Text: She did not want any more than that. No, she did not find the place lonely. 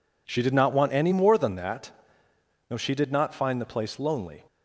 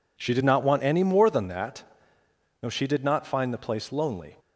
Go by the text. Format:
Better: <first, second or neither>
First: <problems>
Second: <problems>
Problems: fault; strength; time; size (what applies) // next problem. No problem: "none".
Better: neither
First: none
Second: none